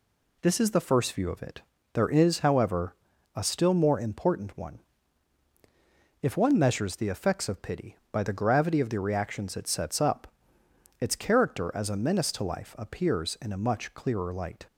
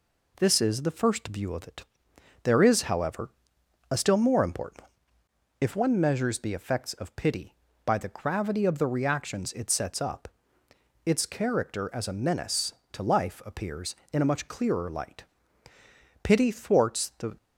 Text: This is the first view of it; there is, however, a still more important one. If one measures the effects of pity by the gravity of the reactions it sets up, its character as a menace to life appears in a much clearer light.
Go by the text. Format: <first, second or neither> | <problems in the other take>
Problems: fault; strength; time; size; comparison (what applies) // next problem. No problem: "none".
first | goes on to say "Pity thwarts the"; noticeable; from 16.2 s on; 1.1 s long